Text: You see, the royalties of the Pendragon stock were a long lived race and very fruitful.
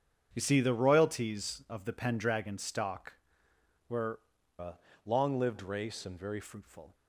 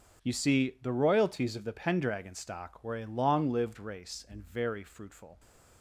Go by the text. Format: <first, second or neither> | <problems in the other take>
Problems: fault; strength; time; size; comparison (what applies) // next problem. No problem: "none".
second | starts louder than the rest; strong; until 1.3 s; 8 dB; also in the second // changes voice from "a" to "very"; from 4.5 to 6.3 s; 1.8 s long // pauses between "a" and "long"; slight; at 4.7 s; 0.28 s long